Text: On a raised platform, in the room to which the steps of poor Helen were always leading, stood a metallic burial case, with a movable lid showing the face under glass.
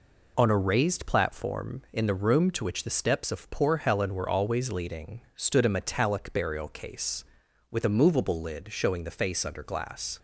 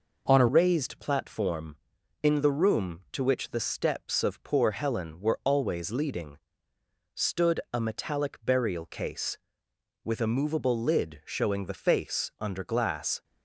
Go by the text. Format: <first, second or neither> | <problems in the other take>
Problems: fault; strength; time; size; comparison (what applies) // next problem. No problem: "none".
first | changes voice at "raised"; from 0.4 s on; 12.8 s long